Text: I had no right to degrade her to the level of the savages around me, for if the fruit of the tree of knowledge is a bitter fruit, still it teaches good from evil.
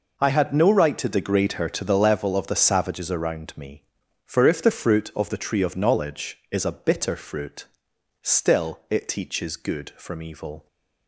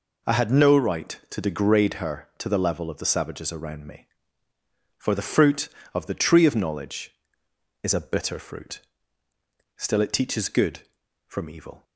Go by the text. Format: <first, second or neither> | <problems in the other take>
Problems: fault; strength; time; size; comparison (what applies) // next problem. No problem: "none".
first | skips "if"; at 5.1 s